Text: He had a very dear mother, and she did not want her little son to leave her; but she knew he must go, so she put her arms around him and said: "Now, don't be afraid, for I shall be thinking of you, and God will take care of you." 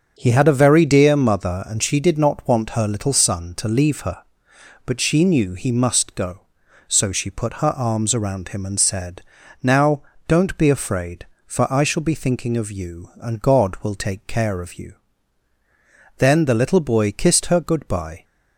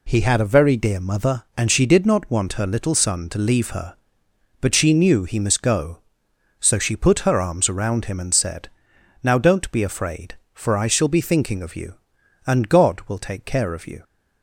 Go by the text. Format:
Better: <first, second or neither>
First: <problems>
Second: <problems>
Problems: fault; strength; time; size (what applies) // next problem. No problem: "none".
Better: second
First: starts louder than the rest; until 1.1 s; 6.5 dB // goes on to say "Then the little boy kissed her goodbye"; strong; from 16.1 s on; 2.0 s long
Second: none